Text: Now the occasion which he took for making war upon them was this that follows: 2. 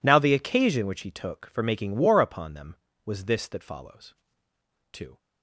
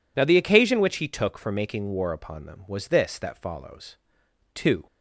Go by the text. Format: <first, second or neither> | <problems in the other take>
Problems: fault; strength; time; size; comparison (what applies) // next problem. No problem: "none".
neither | none